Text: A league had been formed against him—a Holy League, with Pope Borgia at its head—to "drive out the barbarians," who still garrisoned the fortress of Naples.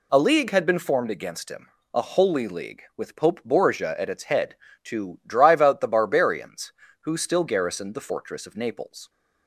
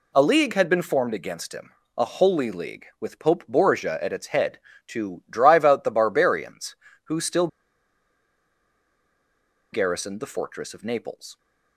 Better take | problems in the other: first | pauses between "still" and "garrisoned"; strong; at 7.4 s; 2.2 s long

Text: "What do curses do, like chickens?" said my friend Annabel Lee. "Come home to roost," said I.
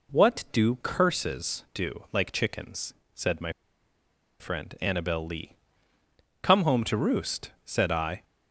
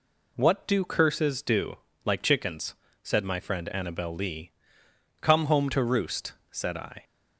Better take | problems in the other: second | pauses between "my" and "friend"; noticeable; at 3.5 s; 0.87 s long

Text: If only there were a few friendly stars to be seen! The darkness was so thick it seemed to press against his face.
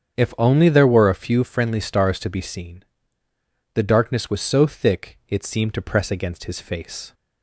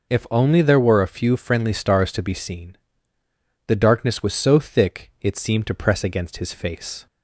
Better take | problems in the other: second | starts louder than the rest; strong; until 1.6 s; 7.5 dB

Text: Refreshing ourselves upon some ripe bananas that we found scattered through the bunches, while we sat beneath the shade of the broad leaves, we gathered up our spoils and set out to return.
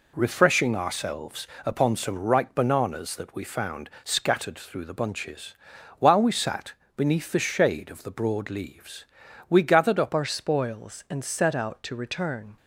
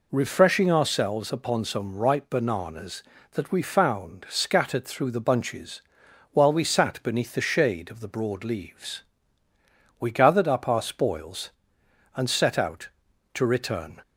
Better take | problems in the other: second | pauses between "ourselves" and "upon"; slight; at 1.4 s; 0.20 s long // pauses between "sat" and "beneath"; slight; at 6.7 s; 0.22 s long // changes voice at "our"; from 10.1 s on; 2.4 s long

